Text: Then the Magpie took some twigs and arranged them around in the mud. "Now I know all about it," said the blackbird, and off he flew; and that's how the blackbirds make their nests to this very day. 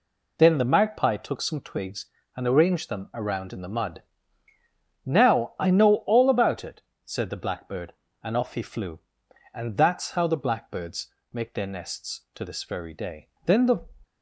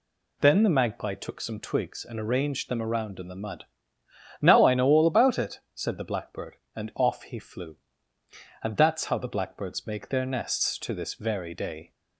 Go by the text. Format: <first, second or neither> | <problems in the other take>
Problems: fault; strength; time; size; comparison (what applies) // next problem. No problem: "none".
second | pauses between "blackbirds" and "make"; slight; at 11.1 s; 0.22 s long // goes on to say "Then the"; slight; from 13.4 s on; 0.42 s long